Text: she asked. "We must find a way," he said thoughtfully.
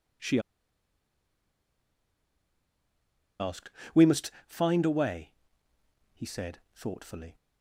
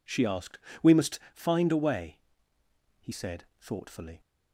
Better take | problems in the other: second | pauses between "she" and "asked"; strong; at 0.3 s; 3.0 s long // pauses between "must" and "find"; slight; at 4.3 s; 0.16 s long; slight in the second

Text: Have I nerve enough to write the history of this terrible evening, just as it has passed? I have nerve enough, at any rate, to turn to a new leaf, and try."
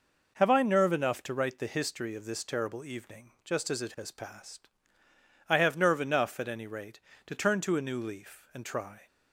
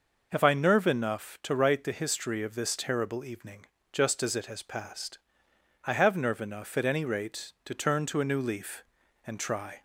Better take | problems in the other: neither | none

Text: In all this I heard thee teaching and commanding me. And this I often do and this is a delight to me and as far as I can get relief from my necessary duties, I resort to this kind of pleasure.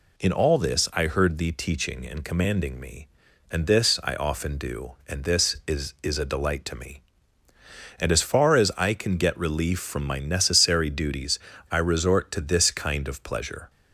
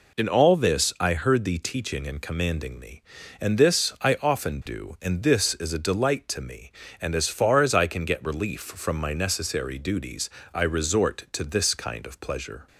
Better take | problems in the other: second | says "is" twice; at 6.0 s

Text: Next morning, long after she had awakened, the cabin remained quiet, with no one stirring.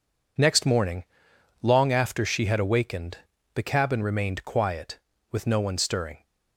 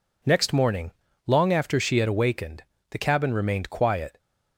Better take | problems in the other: first | stops before "with no one stirring"; at 4.1 s

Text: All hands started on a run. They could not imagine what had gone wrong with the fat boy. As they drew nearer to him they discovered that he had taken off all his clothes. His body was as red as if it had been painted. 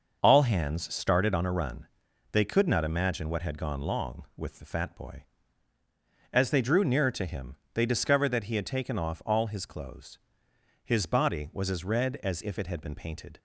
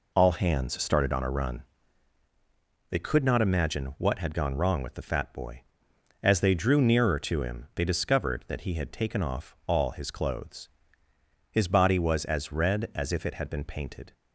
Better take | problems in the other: second | starts louder than the rest; until 1.2 s; 6 dB // says "long" for "wrong"; at 3.8 s // pauses between "him" and "they"; slight; at 7.5 s; 0.18 s long

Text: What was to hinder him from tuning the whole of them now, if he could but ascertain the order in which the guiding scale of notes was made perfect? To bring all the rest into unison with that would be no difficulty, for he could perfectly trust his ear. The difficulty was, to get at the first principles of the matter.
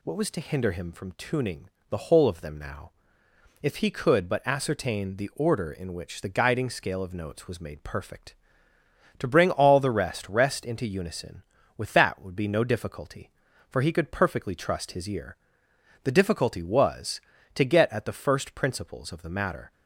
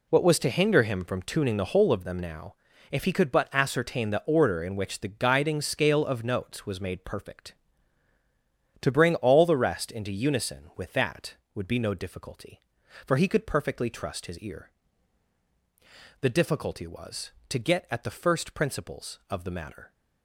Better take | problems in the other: second | pauses between "tuning" and "the"; slight; at 1.6 s; 0.24 s long // says "rest" twice; at 10.2 s

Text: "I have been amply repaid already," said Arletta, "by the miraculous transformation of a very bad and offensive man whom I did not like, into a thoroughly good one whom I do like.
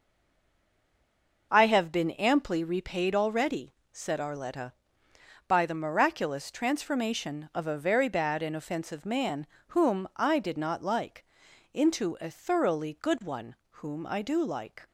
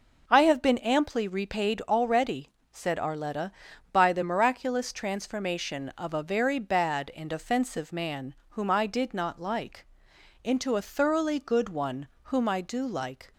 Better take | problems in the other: second | stays silent before the first word; noticeable; until 1.5 s; 1.5 s long // pauses between "man" and "whom"; slight; at 9.4 s; 0.22 s long; slight in the second // pauses between "one" and "whom"; slight; at 13.5 s; 0.16 s long; slight in the second

